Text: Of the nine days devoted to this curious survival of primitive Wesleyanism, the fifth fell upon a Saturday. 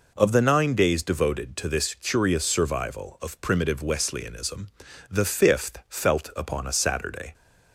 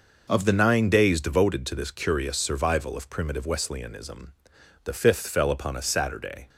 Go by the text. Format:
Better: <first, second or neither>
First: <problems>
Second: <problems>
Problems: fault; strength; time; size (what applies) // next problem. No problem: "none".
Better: second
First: says "felt" for "fell"; at 5.8 s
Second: none